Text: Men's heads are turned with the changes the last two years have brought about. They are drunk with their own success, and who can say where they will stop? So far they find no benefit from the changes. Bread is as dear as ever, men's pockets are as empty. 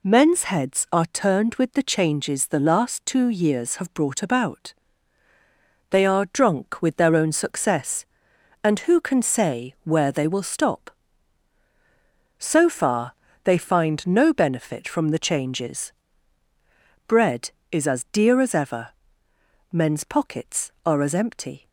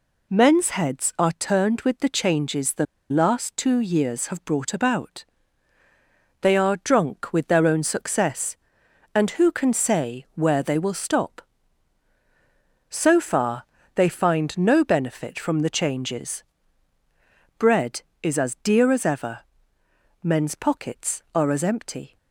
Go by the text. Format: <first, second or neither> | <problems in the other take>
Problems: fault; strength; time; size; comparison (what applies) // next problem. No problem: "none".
first | pauses between "the" and "last"; slight; at 2.8 s; 0.25 s long // pauses between "far" and "they"; slight; at 13.6 s; 0.32 s long; slight in the first